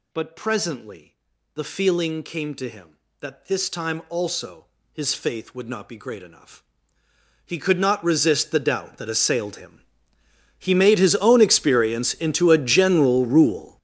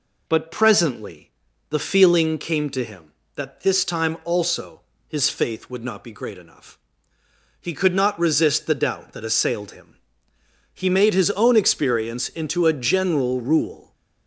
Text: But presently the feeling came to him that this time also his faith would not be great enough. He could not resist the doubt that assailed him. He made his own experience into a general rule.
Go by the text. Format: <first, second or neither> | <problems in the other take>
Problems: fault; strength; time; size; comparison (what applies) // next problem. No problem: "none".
second | gets louder; strong; throughout; 14 dB // pauses between "presently" and "the"; at 1.1 s; 0.38 s long; also in the second // pauses between "also" and "his"; slight; at 4.6 s; 0.28 s long; slight in the second